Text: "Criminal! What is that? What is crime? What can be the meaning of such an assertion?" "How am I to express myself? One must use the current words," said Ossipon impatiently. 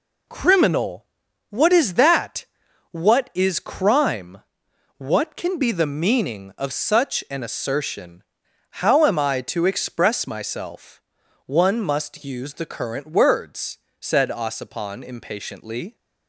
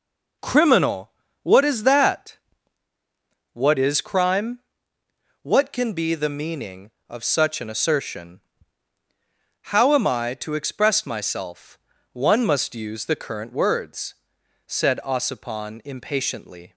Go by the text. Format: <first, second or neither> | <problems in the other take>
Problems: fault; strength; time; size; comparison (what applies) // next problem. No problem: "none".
neither | none